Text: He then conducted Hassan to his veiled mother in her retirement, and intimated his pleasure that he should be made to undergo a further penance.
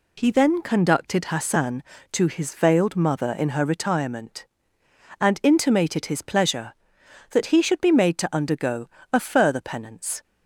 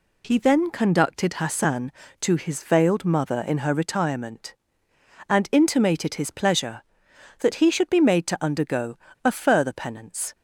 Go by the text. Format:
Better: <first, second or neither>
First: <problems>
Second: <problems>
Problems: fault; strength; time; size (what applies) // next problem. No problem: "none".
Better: neither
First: pauses between "undergo" and "a"; slight; at 8.8 s; 0.24 s long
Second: pauses between "undergo" and "a"; slight; at 8.9 s; 0.27 s long